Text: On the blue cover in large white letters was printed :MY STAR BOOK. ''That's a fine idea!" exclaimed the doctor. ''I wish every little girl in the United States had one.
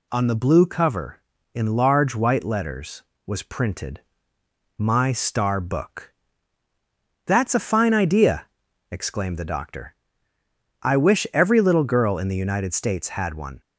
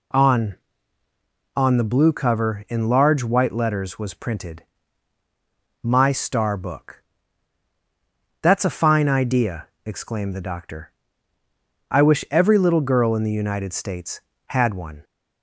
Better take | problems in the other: first | says "On" twice; at 1.5 s

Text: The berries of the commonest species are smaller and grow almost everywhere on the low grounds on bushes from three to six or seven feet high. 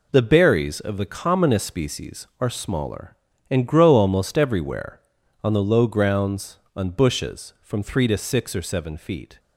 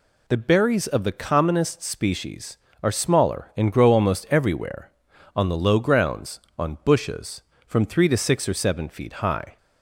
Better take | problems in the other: second | stops before "high"; at 9.3 s

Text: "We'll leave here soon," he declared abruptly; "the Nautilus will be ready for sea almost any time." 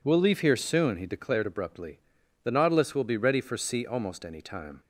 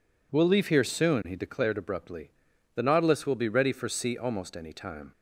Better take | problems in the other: neither | none

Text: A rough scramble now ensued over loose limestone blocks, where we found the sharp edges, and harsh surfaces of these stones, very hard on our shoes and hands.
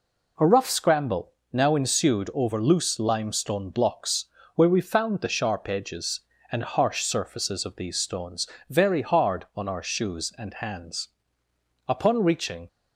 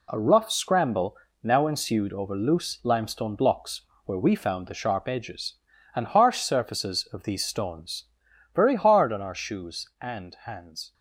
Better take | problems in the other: second | pauses between "scramble" and "now"; slight; at 1.3 s; 0.22 s long; slight in the second // goes on to say "Upon reaching"; noticeable; from 11.8 s on; 0.80 s long

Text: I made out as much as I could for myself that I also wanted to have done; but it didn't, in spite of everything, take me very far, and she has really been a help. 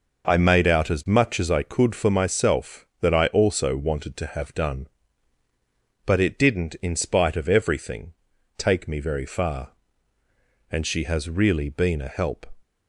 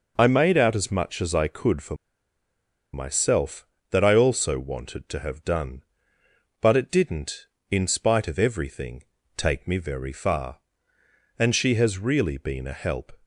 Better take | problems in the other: first | pauses between "for" and "myself"; at 1.9 s; 0.98 s long

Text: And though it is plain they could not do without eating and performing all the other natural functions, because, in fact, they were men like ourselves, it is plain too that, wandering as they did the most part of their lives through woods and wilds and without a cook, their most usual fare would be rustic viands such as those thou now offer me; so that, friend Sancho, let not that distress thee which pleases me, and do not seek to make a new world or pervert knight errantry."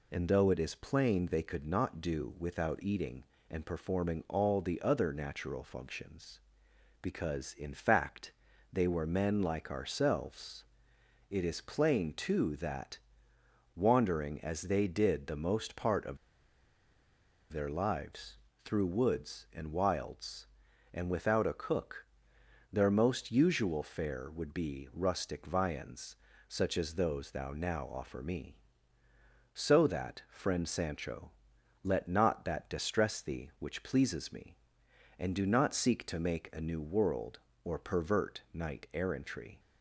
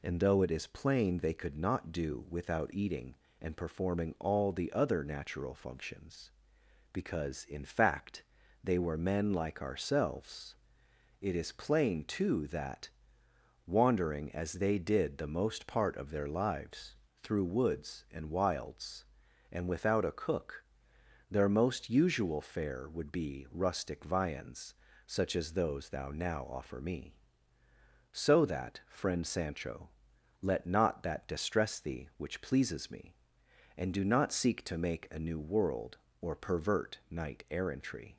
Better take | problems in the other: second | pauses between "of" and "their"; strong; at 16.1 s; 1.3 s long // pauses between "lives" and "through"; slight; at 18.3 s; 0.26 s long; slight in the second // pauses between "viands" and "such"; slight; at 26.1 s; 0.32 s long; slight in the second

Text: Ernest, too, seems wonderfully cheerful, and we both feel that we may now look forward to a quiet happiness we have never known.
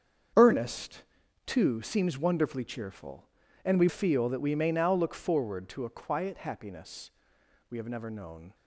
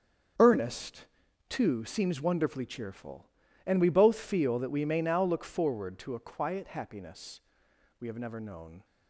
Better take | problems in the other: second | starts louder than the rest; strong; until 1.7 s; 7.5 dB; strong in the second // skips "both"; at 3.8 s // pauses between "happiness" and "we"; noticeable; at 7.0 s; 0.62 s long; noticeable in the second

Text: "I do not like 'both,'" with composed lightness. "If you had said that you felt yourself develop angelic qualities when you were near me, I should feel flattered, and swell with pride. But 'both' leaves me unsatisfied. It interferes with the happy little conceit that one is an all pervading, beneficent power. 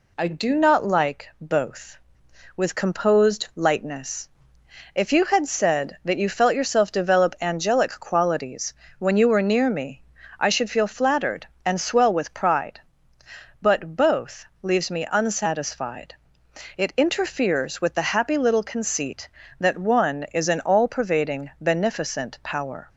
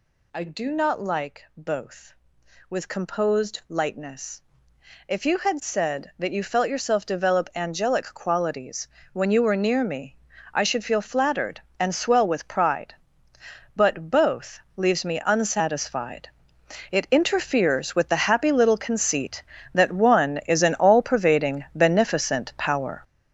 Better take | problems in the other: first | gets louder; strong; throughout; 9 dB // pauses between "qualities" and "when"; slight; at 8.8 s; 0.24 s long; slight in the first // pauses between "both" and "leaves"; slight; at 14.6 s; 0.16 s long; slight in the first

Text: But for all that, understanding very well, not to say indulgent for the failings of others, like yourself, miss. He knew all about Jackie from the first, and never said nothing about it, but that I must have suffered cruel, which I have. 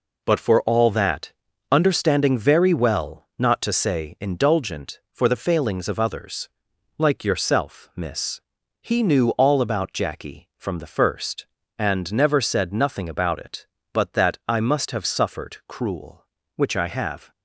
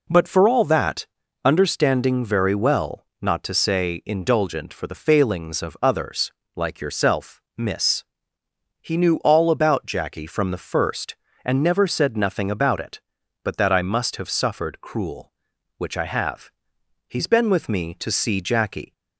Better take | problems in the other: first | goes on to say "He's been with me to see Jackie"; strong; from 17.0 s on; 1.8 s long

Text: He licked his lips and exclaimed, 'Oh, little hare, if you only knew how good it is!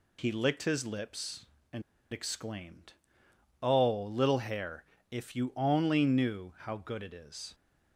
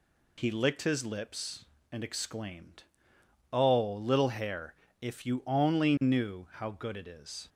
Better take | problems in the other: second | pauses between "and" and "exclaimed"; slight; at 1.8 s; 0.29 s long

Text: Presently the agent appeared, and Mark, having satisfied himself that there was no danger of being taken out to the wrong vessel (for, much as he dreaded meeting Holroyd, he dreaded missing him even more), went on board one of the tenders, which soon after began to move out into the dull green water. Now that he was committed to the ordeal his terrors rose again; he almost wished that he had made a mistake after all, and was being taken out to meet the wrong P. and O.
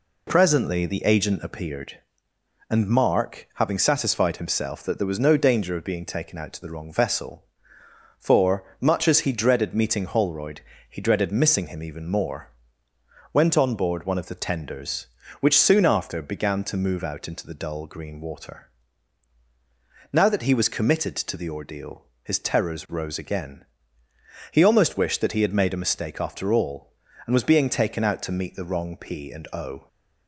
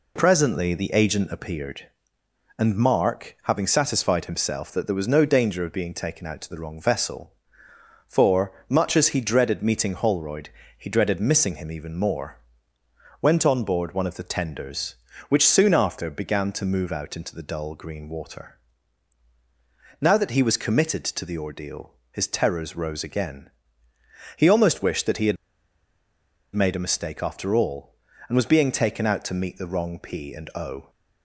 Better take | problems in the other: first | pauses between "ordeal" and "his"; slight; at 21.9 s; 0.18 s long; slight in the first // pauses between "had" and "made"; at 25.3 s; 1.1 s long

